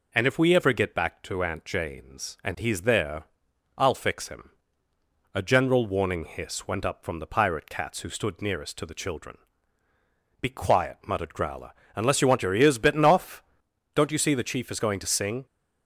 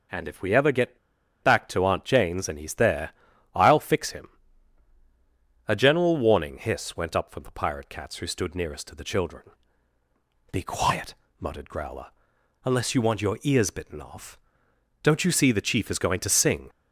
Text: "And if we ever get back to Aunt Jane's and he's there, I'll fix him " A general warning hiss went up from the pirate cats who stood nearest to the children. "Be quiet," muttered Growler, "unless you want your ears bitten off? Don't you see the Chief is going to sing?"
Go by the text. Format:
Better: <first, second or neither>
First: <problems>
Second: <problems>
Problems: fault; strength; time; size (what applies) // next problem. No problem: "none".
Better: first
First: none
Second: pauses between "get" and "back"; at 0.9 s; 0.44 s long